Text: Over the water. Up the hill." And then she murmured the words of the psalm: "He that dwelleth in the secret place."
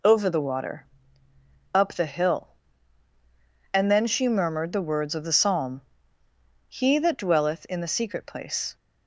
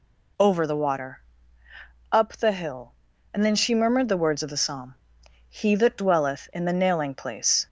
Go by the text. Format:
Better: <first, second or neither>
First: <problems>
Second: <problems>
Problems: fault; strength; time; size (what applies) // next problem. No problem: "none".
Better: first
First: none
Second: says "nailing" for "secret"; at 6.7 s